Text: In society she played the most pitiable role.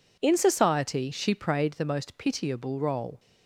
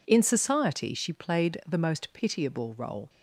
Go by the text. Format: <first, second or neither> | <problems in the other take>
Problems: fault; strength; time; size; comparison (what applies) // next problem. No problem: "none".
second | says "prayed" for "played"; at 1.3 s